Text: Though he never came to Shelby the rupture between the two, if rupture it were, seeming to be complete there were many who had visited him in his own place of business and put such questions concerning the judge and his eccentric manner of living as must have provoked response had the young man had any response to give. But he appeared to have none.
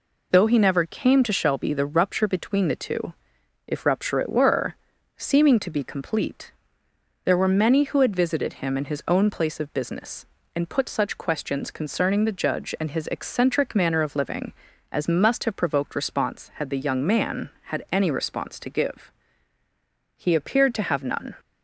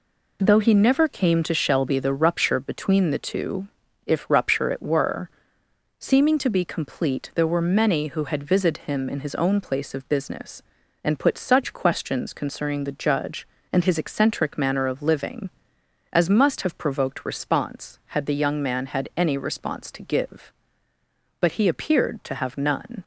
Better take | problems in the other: second | pauses between "complete" and "there"; noticeable; at 6.5 s; 0.72 s long // skips "But"; at 19.6 s

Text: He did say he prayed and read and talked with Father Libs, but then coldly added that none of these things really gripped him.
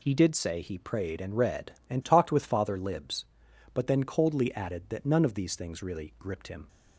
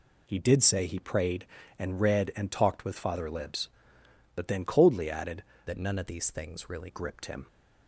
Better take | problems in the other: first | changes voice from "that" to "really"; from 5.6 to 6.8 s; 1.2 s long

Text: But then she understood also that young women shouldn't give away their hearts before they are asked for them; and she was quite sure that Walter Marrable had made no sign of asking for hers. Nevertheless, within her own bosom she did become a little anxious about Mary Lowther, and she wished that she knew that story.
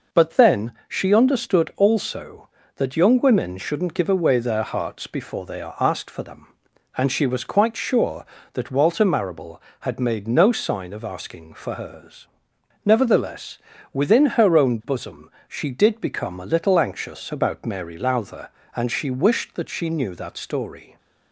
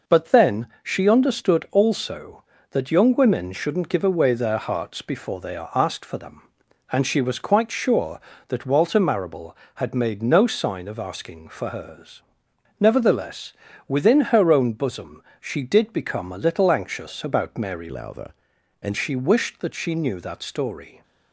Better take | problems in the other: first | pauses between "then" and "she"; slight; at 0.6 s; 0.16 s long; slight in the first // pauses between "bosom" and "she"; slight; at 15.2 s; 0.16 s long; slight in the first // changes voice from "Lowther" to "and"; from 17.8 to 18.9 s; 1.1 s long

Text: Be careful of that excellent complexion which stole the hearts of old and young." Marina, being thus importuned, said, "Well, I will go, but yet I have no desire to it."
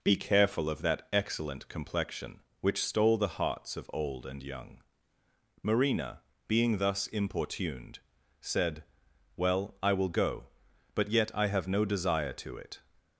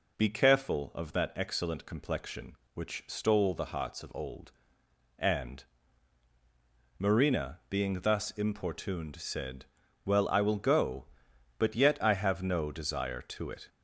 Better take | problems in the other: first | skips "young"; at 6.3 s

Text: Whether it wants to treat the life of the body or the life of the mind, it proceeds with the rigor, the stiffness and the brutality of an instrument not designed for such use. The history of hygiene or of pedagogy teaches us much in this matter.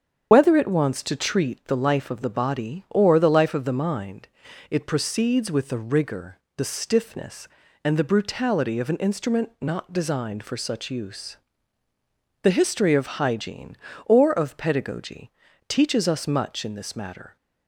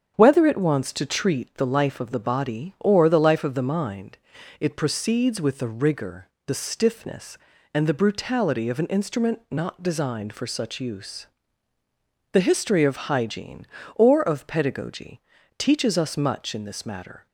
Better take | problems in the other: second | loses the start of "Whether"; at 0.3 s; 50 ms // starts louder than the rest; strong; until 1.3 s; 7.5 dB; also in the second // pauses between "pedagogy" and "teaches"; at 15.3 s; 0.38 s long; also in the second

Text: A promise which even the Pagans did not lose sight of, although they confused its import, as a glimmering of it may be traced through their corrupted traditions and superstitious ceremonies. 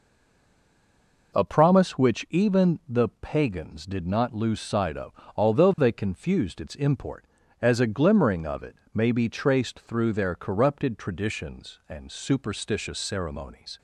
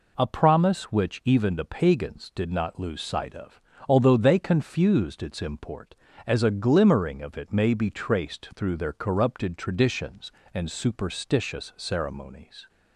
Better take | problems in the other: second | stays silent before the first word; noticeable; until 1.3 s; 1.3 s long // pauses between "it" and "may"; slight; at 8.7 s; 0.18 s long

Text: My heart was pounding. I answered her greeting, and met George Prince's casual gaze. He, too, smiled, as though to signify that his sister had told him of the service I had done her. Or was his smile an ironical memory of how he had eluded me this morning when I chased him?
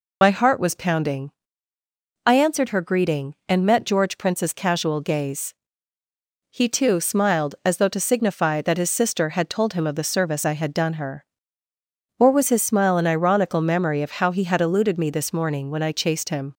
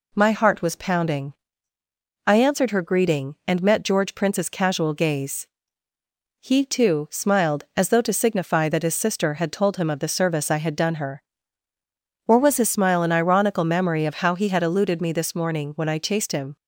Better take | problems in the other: second | loses the start of "My"; at 0.2 s; 50 ms

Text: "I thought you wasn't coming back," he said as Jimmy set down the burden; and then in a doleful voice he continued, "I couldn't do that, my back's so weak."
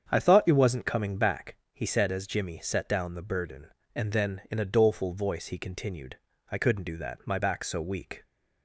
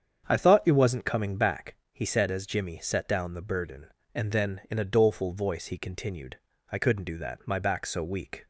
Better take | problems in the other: neither | starts louder than the rest; strong; the same in both

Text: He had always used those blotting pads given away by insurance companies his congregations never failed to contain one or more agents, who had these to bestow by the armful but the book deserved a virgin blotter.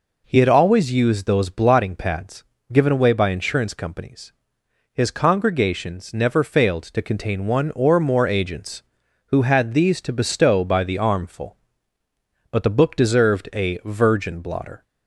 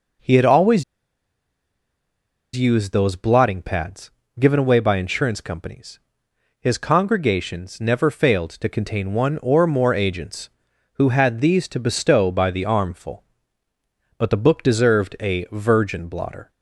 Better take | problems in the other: first | pauses between "always" and "used"; strong; at 0.8 s; 1.7 s long // pauses between "pads" and "given"; slight; at 4.1 s; 0.28 s long; slight in the first // pauses between "companies" and "his"; noticeable; at 5.9 s; 0.62 s long; noticeable in the first

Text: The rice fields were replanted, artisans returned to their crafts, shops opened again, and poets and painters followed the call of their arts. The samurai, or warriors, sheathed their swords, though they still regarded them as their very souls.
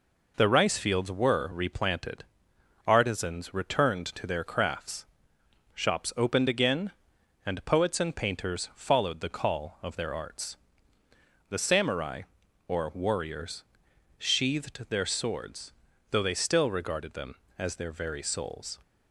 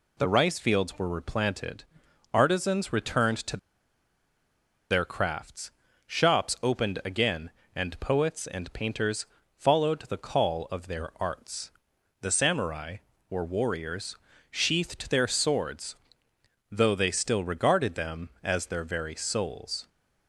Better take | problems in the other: first | pauses between "to" and "their"; strong; at 3.5 s; 1.3 s long // pauses between "painters" and "followed"; slight; at 9.2 s; 0.32 s long

